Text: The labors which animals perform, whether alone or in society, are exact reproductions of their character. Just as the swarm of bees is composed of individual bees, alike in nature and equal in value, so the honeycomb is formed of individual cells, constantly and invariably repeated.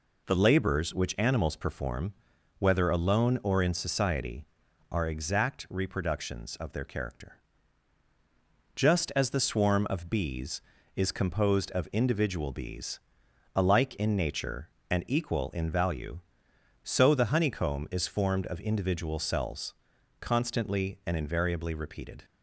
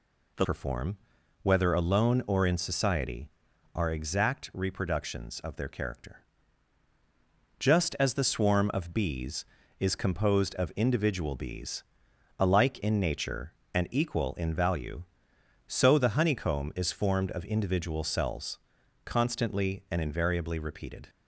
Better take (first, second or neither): first